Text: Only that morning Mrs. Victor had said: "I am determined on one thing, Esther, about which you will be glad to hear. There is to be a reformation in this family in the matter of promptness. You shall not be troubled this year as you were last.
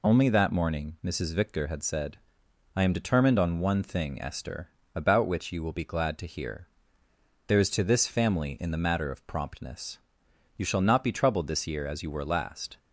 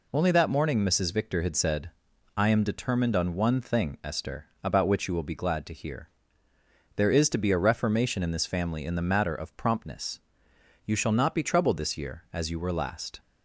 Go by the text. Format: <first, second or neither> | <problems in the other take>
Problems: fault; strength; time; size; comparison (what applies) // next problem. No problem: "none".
second | skips "be a reformation in"; at 7.8 s